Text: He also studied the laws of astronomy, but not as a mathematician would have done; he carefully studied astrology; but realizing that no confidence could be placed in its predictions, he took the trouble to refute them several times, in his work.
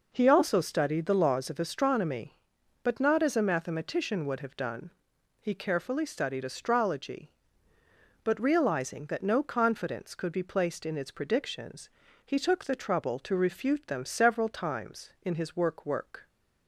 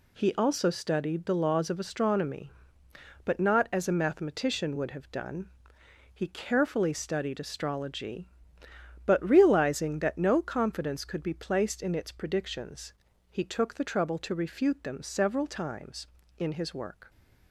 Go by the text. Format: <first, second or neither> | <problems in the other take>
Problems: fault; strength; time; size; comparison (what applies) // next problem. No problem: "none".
second | says "work" twice; at 15.8 s